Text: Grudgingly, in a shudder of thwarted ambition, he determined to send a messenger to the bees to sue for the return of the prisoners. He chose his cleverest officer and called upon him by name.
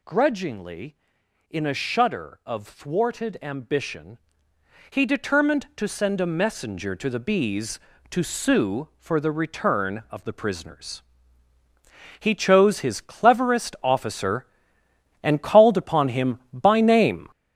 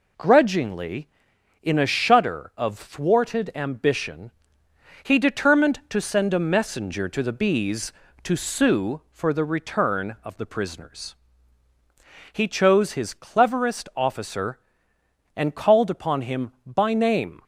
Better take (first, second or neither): second